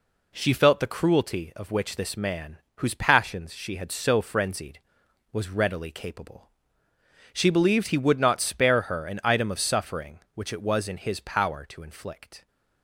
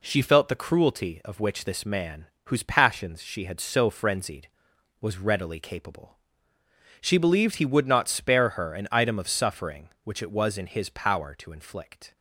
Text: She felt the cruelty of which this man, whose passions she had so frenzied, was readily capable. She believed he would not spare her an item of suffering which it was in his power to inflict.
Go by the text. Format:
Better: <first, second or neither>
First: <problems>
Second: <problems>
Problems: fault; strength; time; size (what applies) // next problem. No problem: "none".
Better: neither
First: none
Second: none